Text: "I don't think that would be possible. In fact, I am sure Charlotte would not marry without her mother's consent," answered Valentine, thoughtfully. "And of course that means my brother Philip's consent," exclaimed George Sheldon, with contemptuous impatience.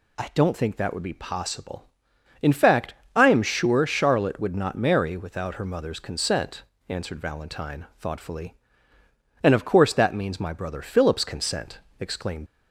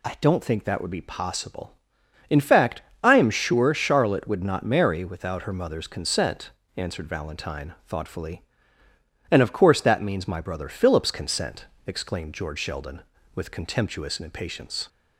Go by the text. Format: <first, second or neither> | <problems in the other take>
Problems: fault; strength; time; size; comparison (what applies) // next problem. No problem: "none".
second | stops before "George Sheldon with contemptuous impatience"; at 12.4 s